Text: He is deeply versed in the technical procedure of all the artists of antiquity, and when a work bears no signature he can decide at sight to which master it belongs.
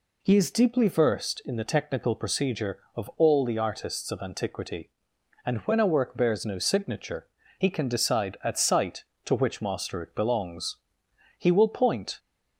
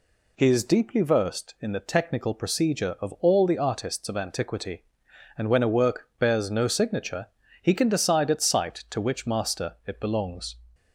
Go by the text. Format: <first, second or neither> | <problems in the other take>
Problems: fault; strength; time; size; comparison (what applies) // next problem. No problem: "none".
second | pauses between "signature" and "he"; slight; at 7.2 s; 0.30 s long; slight in the second // goes on to say "He will point"; noticeable; from 11.3 s on; 0.80 s long